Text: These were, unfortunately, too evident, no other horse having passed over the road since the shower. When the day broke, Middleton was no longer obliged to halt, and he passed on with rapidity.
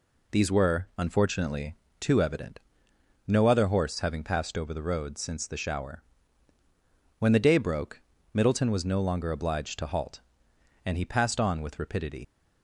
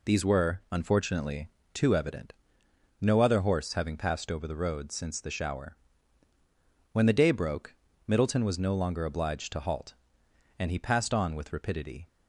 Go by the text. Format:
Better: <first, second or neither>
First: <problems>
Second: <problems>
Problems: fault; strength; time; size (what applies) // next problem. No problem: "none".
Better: second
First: leaves "rapidity" unfinished; at 12.2 s; 90 ms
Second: none